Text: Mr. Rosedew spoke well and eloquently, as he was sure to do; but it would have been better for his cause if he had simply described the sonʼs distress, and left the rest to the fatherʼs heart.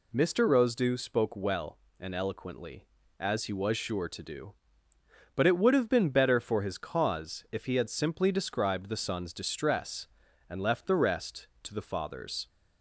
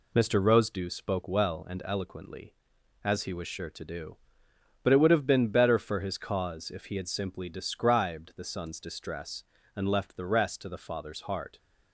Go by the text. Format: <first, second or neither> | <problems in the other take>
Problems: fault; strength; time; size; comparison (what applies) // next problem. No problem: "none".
second | stops before "heart"; at 12.4 s